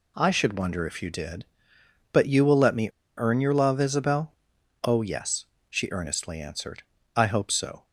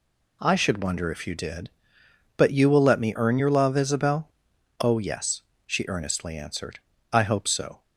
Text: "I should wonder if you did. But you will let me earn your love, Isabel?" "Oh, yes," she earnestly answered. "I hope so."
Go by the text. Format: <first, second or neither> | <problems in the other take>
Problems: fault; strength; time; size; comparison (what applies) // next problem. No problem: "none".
second | pauses between "me" and "earn"; slight; at 2.8 s; 0.29 s long